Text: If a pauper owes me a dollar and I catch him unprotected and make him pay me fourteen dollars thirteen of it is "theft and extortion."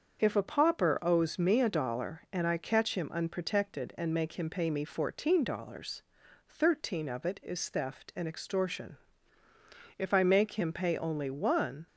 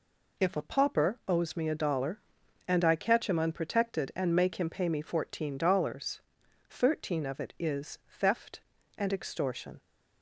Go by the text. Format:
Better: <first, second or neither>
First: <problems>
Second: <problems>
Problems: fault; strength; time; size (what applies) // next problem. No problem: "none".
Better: second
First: starts louder than the rest; until 1.2 s; 6.5 dB // pauses between "dollars" and "thirteen"; at 6.0 s; 0.44 s long // goes on to say "If I make him pay only one"; strong; from 9.9 s on; 1.9 s long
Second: pauses between "dollars" and "thirteen"; noticeable; at 6.2 s; 0.48 s long